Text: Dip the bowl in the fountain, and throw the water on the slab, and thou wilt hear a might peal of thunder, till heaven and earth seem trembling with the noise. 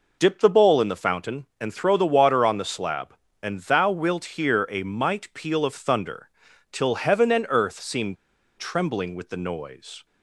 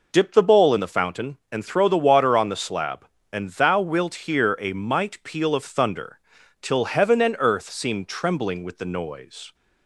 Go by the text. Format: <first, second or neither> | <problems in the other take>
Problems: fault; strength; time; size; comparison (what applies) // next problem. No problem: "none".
second | pauses between "seem" and "trembling"; at 8.1 s; 0.43 s long